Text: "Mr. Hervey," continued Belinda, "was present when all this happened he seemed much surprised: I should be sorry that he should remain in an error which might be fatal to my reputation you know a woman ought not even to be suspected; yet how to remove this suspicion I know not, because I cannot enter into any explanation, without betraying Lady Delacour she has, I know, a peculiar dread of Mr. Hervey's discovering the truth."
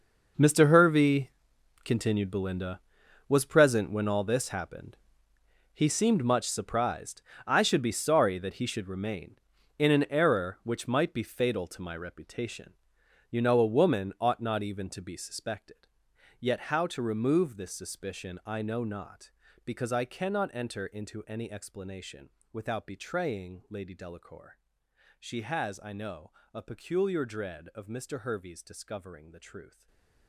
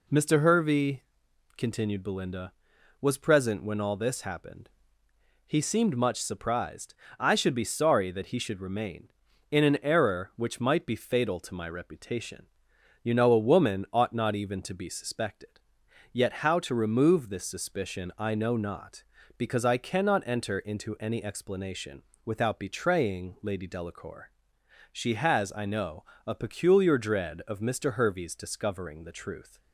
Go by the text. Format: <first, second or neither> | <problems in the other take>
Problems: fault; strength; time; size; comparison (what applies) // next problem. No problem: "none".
second | gets quieter; strong; throughout; 15 dB // pauses between "happened" and "he"; noticeable; at 4.9 s; 0.80 s long; noticeable in the second // pauses between "reputation" and "you"; noticeable; at 12.7 s; 0.56 s long; noticeable in the second // pauses between "Delacour" and "she"; noticeable; at 24.5 s; 0.62 s long; noticeable in the second // stays silent after the last word; slight; from 29.6 s on; 0.6 s long